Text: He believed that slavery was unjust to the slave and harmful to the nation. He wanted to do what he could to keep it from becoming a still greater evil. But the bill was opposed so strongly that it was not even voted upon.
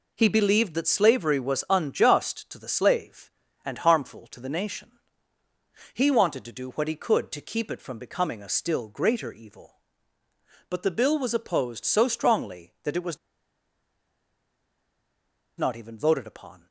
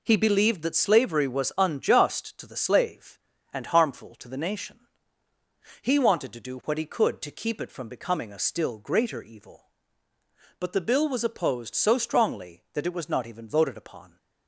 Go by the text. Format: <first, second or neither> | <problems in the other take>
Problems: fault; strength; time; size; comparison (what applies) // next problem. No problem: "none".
second | pauses between "was" and "not"; strong; at 13.1 s; 2.4 s long